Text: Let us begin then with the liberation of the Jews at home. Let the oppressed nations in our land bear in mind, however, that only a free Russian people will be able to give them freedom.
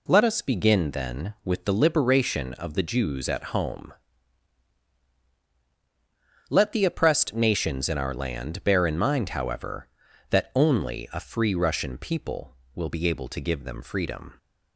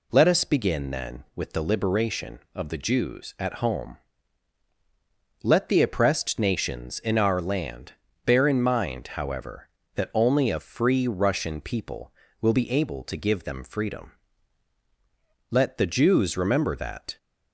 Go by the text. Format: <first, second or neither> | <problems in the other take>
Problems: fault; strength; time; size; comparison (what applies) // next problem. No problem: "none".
first | pauses between "land" and "bear"; slight; at 7.9 s; 0.32 s long // goes on to say "Let the Jews remember that"; from 15.5 s on; 1.6 s long